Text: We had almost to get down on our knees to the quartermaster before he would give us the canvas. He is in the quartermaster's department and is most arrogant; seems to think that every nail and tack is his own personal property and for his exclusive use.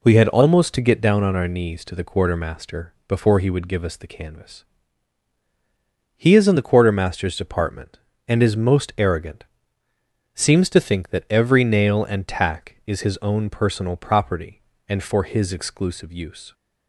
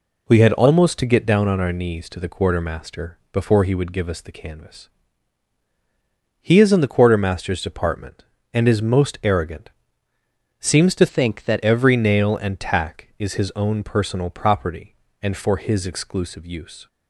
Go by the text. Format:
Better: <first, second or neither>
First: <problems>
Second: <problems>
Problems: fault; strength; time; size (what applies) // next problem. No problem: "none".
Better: first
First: none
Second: changes voice from "think" to "that"; from 11.0 to 11.6 s; 0.6 s long